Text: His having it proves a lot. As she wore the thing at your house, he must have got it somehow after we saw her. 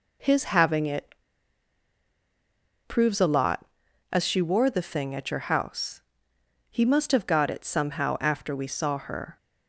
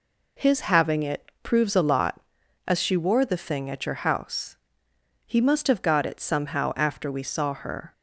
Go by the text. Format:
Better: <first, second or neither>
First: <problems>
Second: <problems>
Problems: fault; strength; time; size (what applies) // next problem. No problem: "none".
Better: second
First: pauses between "it" and "proves"; strong; at 1.1 s; 1.7 s long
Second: none